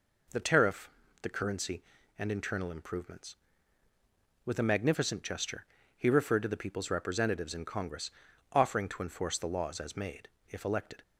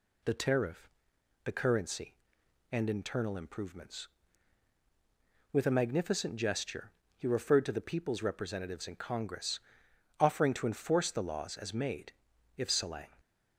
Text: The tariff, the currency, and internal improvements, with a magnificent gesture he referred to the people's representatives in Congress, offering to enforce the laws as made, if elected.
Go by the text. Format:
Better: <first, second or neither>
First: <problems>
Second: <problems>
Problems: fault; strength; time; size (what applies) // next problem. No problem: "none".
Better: first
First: pauses between "gesture" and "he"; slight; at 5.6 s; 0.32 s long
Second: pauses between "gesture" and "he"; slight; at 6.9 s; 0.24 s long // says "salang" for "elected"; at 12.6 s